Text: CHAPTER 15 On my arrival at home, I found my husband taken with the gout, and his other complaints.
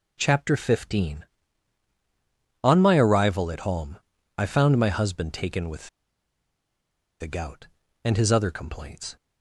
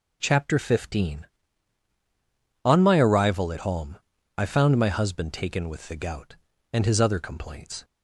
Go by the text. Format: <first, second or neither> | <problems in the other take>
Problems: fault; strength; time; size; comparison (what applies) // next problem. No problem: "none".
second | pauses between "with" and "the"; strong; at 5.8 s; 1.3 s long